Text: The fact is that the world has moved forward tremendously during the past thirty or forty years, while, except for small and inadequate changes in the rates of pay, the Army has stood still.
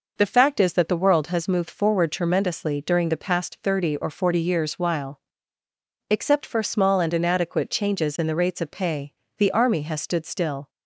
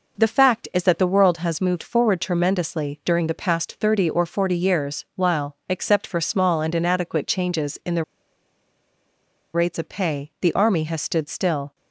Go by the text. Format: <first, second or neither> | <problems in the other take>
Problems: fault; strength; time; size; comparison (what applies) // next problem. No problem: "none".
first | pauses between "the" and "rates"; strong; at 8.0 s; 1.5 s long